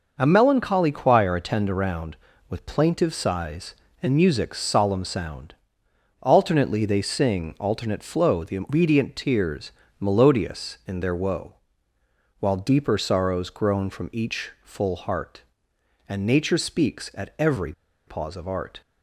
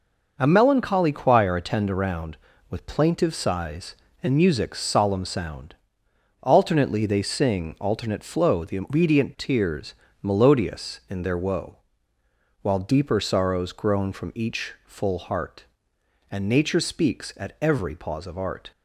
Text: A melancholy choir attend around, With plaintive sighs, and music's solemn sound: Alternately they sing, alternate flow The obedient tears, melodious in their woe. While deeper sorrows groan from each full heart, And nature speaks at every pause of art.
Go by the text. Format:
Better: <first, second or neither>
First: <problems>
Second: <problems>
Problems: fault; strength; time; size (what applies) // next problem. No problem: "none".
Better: second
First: pauses between "every" and "pause"; slight; at 17.7 s; 0.34 s long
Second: none